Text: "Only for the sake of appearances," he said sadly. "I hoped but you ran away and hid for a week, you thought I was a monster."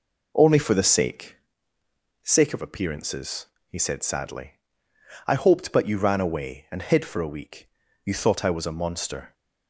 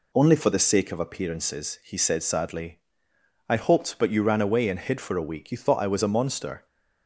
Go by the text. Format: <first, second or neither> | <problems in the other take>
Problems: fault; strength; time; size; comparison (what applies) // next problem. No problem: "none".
second | says "sake" twice; at 2.2 s